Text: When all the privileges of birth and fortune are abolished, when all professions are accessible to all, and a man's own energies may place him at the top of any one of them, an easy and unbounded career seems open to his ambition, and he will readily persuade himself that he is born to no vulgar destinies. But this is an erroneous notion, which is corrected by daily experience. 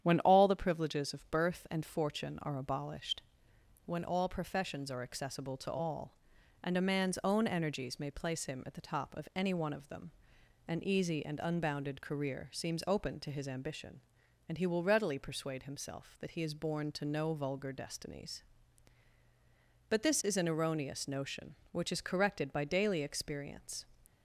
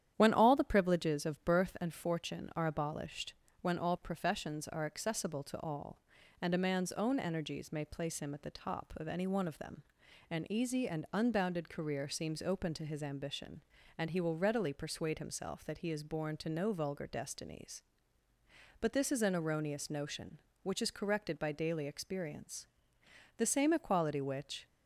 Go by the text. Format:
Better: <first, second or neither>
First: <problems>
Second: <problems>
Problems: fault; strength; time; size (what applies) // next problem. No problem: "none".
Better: first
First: starts louder than the rest; strong; until 1.0 s; 9.5 dB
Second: starts louder than the rest; strong; until 1.1 s; 10 dB // goes on to say "The same equality which"; noticeable; from 23.3 s on; 1.2 s long